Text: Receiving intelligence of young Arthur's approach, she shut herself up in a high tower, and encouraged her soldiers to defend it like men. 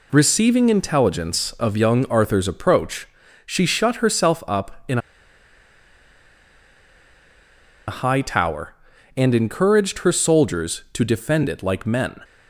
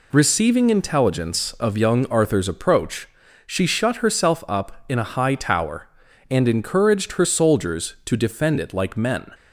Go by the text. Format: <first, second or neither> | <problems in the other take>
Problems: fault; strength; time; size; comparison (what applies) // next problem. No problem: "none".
second | pauses between "in" and "a"; strong; at 4.9 s; 2.8 s long